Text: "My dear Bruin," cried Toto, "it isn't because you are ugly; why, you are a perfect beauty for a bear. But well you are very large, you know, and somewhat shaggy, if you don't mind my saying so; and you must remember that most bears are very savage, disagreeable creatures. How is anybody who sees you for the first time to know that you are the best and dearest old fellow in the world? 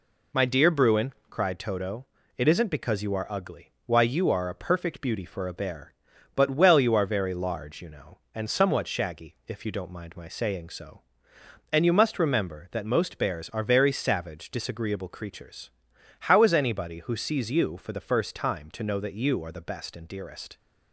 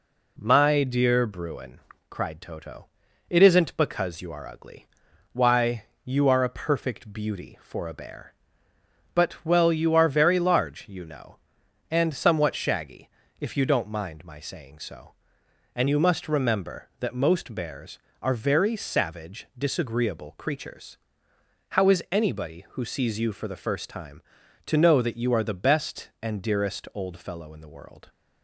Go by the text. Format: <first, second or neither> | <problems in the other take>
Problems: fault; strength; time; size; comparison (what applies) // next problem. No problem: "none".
second | stops before "old fellow in the world"; at 20.5 s